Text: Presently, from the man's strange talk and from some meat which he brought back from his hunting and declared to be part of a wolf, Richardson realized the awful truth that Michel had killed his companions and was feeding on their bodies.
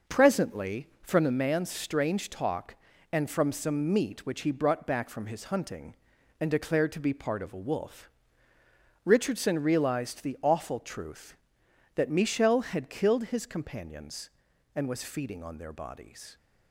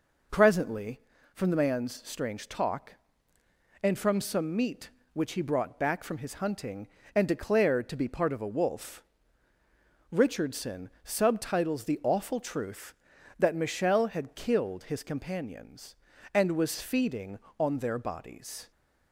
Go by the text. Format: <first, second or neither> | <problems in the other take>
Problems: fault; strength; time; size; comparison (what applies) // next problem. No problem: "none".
first | says "subtitles" for "realized"; at 11.0 s